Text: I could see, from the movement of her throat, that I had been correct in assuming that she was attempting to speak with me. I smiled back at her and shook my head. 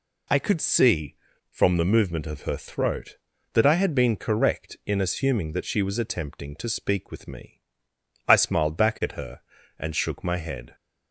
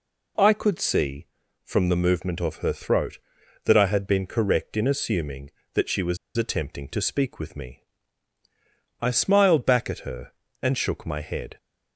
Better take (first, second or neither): first